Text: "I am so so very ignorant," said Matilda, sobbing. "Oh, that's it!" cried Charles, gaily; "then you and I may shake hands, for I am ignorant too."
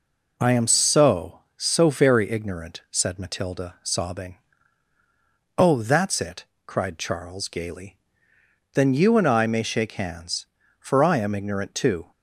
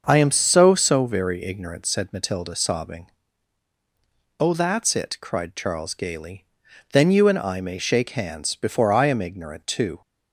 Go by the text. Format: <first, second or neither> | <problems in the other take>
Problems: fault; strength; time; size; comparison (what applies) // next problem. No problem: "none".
first | starts louder than the rest; until 1.0 s; 6.5 dB // says "before" for "for"; at 8.5 s